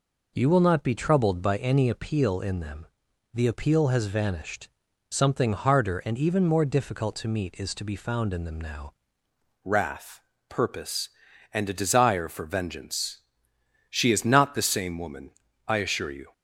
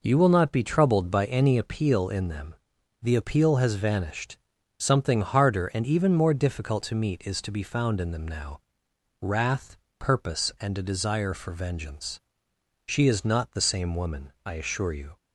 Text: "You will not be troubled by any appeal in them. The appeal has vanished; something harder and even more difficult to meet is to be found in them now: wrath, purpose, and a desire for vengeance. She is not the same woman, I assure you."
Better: second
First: changes voice at "wrath"; from 9.6 s on; 6.7 s long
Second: none

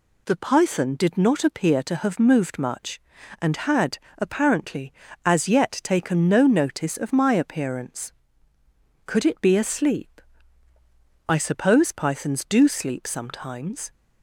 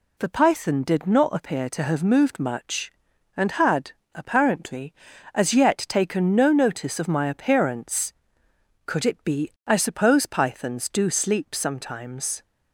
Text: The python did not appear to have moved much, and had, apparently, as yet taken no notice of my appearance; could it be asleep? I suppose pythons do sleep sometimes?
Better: first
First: none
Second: skips "asleep"; at 9.5 s

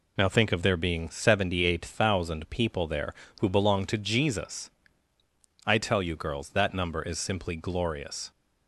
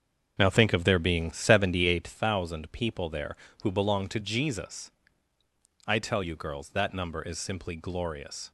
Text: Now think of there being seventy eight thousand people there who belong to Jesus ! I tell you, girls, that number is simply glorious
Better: first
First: none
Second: starts louder than the rest; until 2.1 s; 7 dB

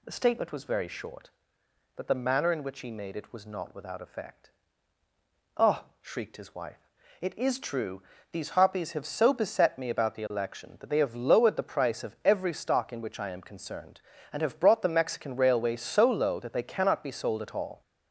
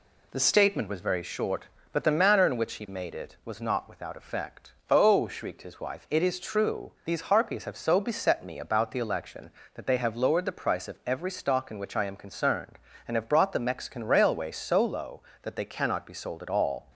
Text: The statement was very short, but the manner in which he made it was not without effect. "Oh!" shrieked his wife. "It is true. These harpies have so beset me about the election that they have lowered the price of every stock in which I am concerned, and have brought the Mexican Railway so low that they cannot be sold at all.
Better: neither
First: none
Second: none

